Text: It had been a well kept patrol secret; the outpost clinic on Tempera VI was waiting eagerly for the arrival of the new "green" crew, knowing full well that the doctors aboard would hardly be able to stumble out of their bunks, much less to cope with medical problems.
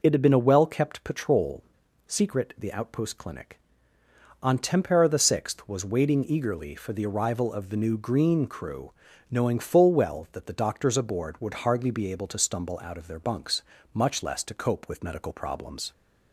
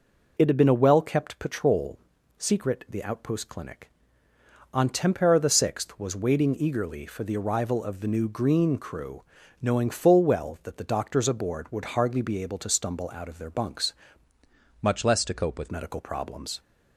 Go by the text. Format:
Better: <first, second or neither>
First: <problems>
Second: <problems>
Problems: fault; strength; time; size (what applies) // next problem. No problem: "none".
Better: first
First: pauses between "patrol" and "secret"; at 1.6 s; 0.44 s long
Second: pauses between "patrol" and "secret"; at 1.9 s; 0.40 s long // changes voice from "much" to "with"; from 14.8 to 15.6 s; 0.8 s long